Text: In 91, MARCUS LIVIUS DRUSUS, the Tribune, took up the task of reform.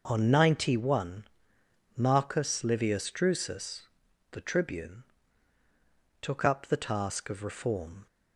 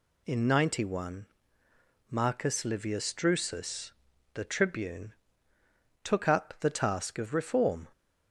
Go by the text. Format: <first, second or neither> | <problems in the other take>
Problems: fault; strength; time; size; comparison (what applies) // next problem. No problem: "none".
second | says "On" for "In"; at 0.0 s